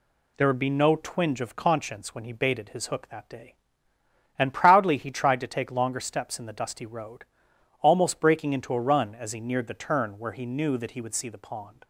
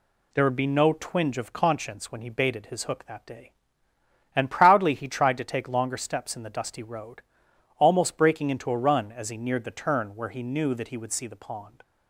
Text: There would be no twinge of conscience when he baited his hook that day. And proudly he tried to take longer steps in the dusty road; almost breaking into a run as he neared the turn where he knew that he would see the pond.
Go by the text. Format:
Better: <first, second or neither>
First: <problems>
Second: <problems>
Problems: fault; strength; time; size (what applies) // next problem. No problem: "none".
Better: neither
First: none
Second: none